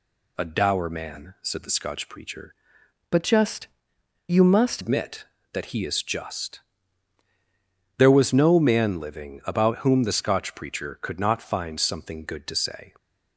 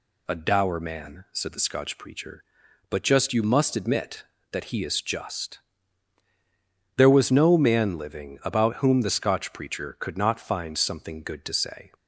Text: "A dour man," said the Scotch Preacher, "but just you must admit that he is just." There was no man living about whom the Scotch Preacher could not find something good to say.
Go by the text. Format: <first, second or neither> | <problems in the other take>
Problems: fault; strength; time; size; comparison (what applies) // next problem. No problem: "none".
second | changes voice from "but" to "must"; from 3.1 to 4.8 s; 1.7 s long // pauses between "just" and "you"; noticeable; at 3.6 s; 0.60 s long